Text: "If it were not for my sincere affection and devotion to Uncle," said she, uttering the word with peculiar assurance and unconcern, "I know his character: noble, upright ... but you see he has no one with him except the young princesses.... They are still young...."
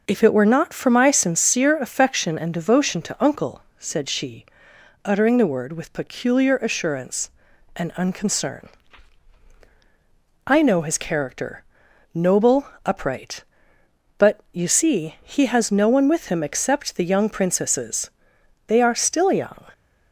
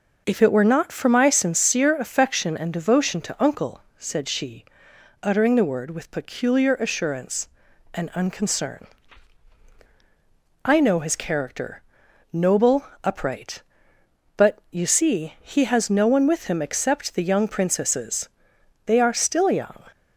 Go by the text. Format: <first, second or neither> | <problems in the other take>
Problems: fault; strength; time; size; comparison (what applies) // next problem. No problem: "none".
neither | none